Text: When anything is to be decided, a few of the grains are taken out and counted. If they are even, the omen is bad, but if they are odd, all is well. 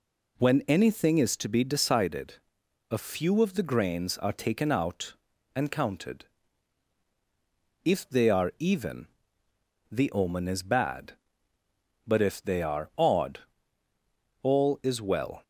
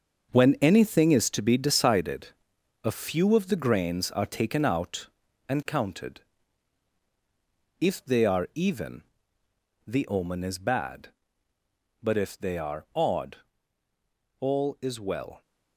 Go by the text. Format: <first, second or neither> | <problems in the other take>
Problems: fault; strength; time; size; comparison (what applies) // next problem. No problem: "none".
first | gets quieter; strong; throughout; 8.5 dB